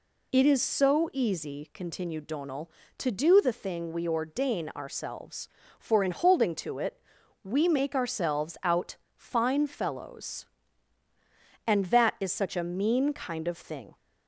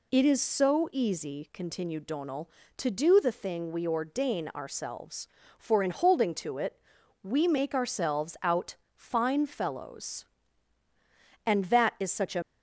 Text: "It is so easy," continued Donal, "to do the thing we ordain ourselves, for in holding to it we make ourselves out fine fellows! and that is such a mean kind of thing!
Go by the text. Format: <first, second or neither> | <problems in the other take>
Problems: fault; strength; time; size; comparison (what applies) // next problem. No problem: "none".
first | pauses between "it" and "we"; at 6.8 s; 0.40 s long; also in the first // pauses between "out" and "fine"; slight; at 8.7 s; 0.20 s long; slight in the first // stops before "mean kind of thing"; at 12.4 s